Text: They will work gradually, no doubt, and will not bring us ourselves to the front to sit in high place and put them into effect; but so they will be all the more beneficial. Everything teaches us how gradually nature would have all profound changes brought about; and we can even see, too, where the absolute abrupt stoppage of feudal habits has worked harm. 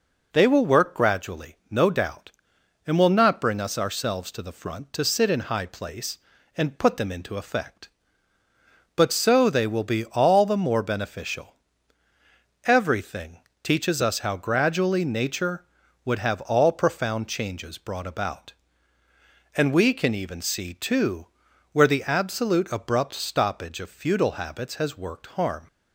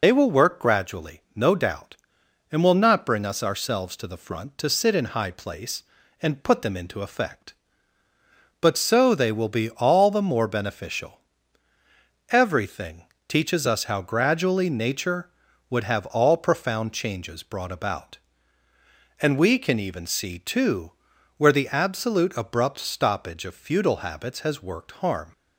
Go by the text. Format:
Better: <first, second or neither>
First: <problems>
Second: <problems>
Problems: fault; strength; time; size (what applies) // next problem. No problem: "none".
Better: first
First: pauses between "Everything" and "teaches"; slight; at 13.3 s; 0.24 s long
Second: loses the start of "They"; at 0.0 s; 50 ms // pauses between "Everything" and "teaches"; slight; at 13.0 s; 0.24 s long